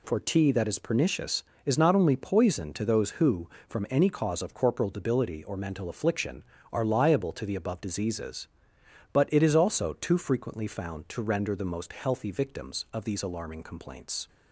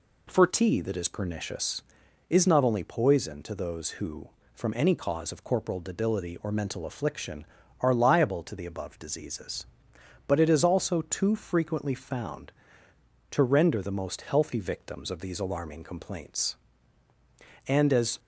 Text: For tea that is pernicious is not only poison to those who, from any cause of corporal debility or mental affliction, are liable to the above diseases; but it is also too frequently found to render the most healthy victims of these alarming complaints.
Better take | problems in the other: first | goes on to say "And as"; from 17.6 s on; 0.52 s long

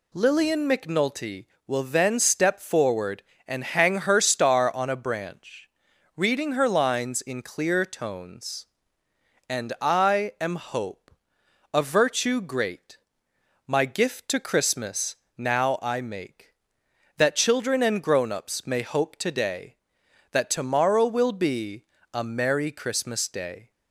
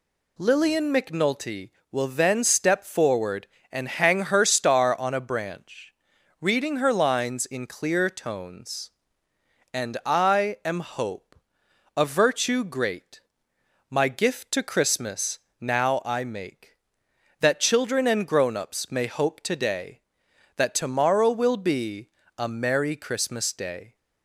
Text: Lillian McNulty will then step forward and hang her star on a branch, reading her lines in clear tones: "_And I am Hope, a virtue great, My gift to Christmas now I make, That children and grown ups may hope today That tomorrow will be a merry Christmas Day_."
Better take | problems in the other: neither | pauses between "Christmas" and "now"; slight; the same in both // pauses between "be" and "a"; slight; the same in both

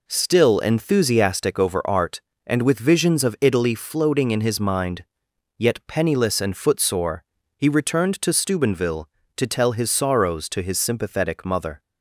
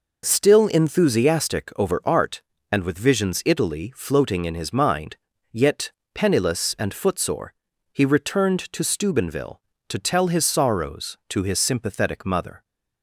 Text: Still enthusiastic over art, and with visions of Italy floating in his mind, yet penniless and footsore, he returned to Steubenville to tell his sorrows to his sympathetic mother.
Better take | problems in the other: first | skips "of"; at 3.4 s // pauses between "yet" and "penniless"; slight; at 5.9 s; 0.22 s long

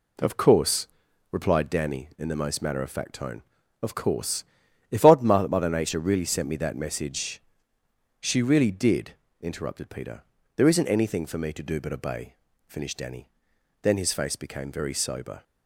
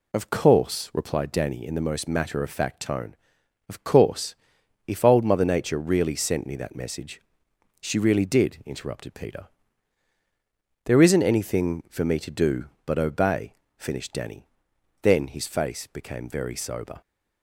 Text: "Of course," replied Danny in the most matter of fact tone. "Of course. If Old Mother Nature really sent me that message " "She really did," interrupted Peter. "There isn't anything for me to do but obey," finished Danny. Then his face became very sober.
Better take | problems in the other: second | says "Odd" for "Old"; at 5.0 s

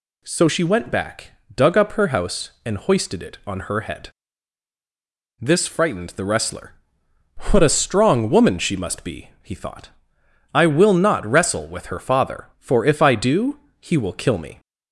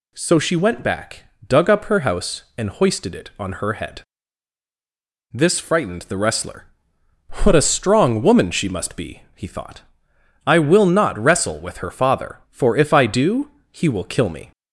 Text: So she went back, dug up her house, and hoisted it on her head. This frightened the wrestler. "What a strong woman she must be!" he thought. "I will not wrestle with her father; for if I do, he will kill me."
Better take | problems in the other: neither | none

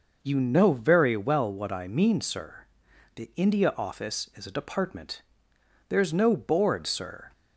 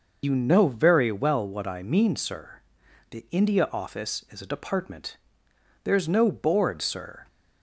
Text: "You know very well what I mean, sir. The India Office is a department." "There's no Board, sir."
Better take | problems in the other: first | loses the start of "You"; at 0.2 s; 65 ms

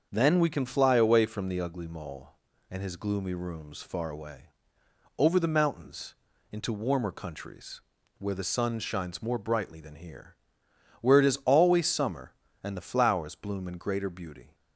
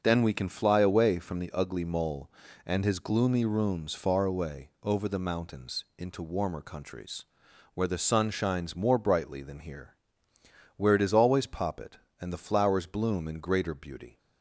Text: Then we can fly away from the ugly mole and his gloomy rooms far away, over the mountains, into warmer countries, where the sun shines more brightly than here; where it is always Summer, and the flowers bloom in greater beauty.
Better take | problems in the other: first | starts louder than the rest; noticeable; until 1.0 s; 6 dB; also in the first // says "Poppet" for "Summer"; at 11.4 s

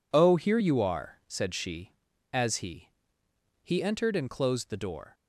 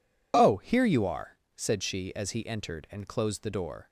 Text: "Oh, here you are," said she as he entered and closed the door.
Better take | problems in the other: second | says "he" twice; at 3.6 s

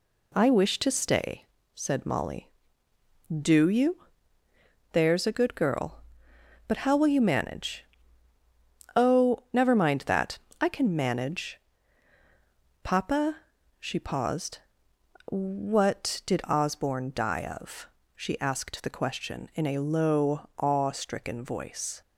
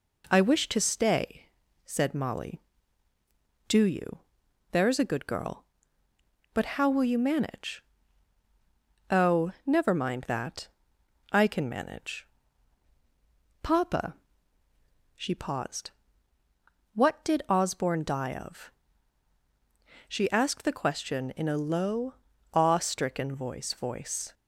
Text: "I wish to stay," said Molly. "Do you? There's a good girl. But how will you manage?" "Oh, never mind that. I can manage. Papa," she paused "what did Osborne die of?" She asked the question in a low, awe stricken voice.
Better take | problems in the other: first | pauses between "paused" and "what"; at 15.9 s; 1.0 s long; noticeable in the first // says "voice" twice; at 23.7 s

